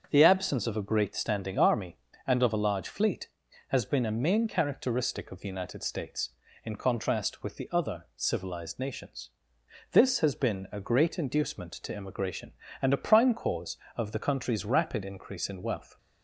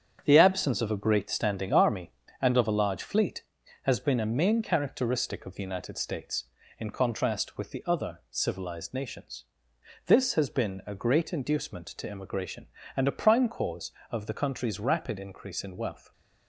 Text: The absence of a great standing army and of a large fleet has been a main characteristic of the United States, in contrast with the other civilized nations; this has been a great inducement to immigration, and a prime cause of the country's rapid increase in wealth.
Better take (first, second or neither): first